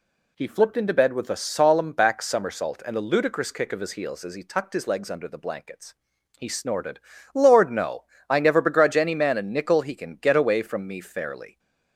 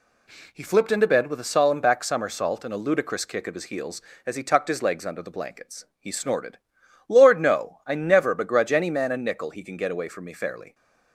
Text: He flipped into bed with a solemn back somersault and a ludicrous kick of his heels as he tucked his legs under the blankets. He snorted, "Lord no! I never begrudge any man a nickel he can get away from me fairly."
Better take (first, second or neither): neither